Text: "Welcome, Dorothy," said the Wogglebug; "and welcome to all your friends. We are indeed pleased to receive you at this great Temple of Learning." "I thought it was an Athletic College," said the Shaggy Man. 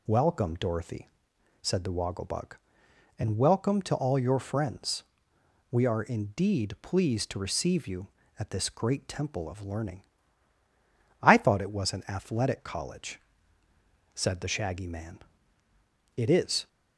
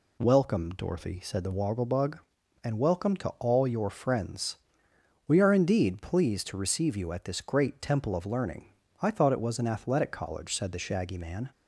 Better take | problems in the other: second | goes on to say "It is"; from 16.1 s on; 0.52 s long

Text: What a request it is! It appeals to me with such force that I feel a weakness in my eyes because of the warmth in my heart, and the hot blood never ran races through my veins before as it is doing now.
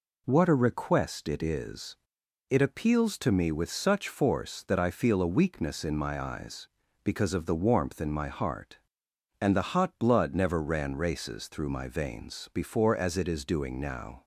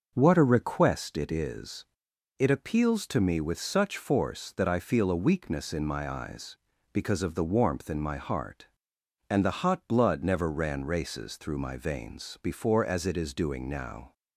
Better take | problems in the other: first | starts louder than the rest; noticeable; until 1.2 s; 6 dB

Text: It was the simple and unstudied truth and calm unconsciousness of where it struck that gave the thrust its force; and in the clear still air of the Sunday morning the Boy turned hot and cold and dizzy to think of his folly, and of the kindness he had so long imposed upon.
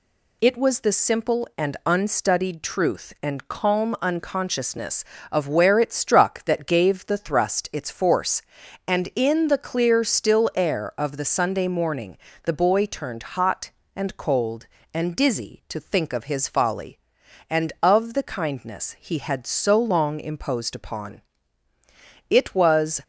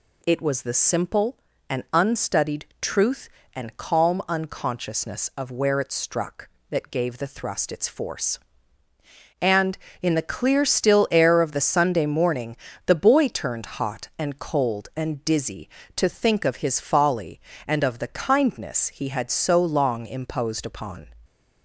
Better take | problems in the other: second | pauses between "morning" and "the"; slight; at 12.1 s; 0.26 s long; slight in the second // pauses between "turned" and "hot"; slight; at 13.2 s; 0.18 s long // goes on to say "It was"; noticeable; from 22.2 s on; 0.70 s long

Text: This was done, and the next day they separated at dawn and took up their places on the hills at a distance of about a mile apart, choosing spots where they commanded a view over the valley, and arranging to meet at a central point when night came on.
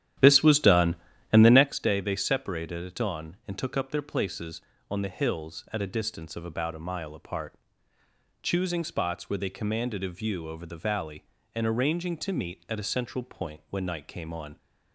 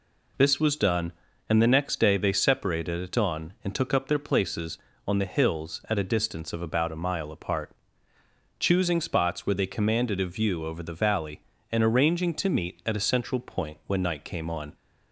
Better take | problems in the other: second | starts louder than the rest; strong; until 1.7 s; 11 dB

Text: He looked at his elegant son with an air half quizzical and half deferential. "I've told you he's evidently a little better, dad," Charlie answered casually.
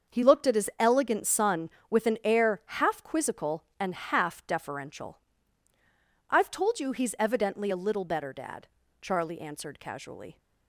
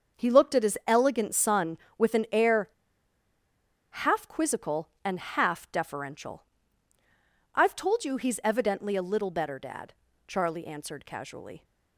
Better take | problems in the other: first | starts louder than the rest; until 1.2 s; 6.5 dB; also in the first // pauses between "air" and "half"; at 2.6 s; 1.2 s long

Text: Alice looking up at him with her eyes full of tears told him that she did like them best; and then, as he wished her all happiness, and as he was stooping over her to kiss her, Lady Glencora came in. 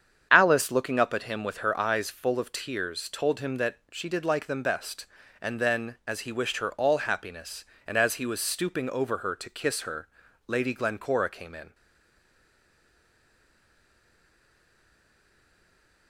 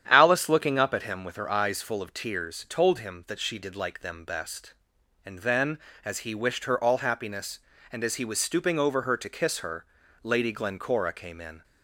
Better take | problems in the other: second | starts louder than the rest; strong; until 1.3 s; 8 dB; strong in the second // pauses between "that" and "she"; slight; at 3.7 s; 0.16 s long // stays silent after the last word; strong; from 11.7 s on; 4.3 s long

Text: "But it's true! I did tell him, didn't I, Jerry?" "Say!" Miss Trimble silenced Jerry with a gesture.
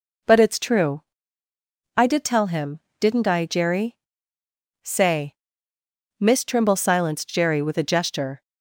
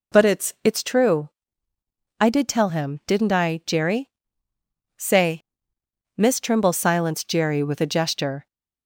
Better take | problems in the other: first | says "it's" twice; at 0.6 s

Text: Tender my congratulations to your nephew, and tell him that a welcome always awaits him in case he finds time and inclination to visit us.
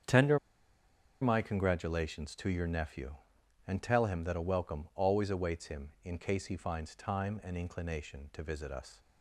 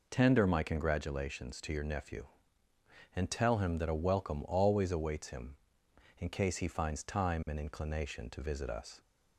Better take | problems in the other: second | starts louder than the rest; strong; until 1.9 s; 8 dB // pauses between "Tender" and "my"; noticeable; at 0.3 s; 0.84 s long

